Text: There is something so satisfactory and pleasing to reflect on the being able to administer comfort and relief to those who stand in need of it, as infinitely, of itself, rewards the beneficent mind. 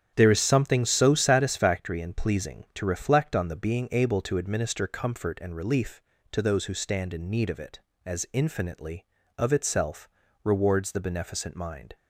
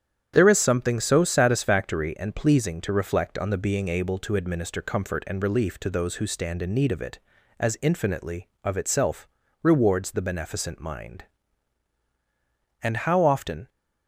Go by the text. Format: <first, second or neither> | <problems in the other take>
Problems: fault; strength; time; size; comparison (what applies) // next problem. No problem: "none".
first | starts louder than the rest; strong; until 1.3 s; 9 dB; strong in the first // goes on to say "And how often"; noticeable; from 12.8 s on; 0.86 s long